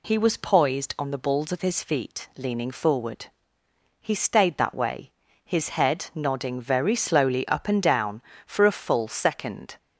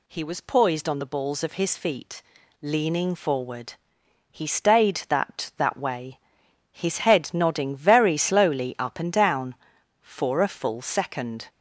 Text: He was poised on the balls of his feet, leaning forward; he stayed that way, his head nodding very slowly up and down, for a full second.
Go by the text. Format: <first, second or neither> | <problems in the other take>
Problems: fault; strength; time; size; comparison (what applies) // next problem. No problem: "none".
first | says "that" twice; at 5.5 s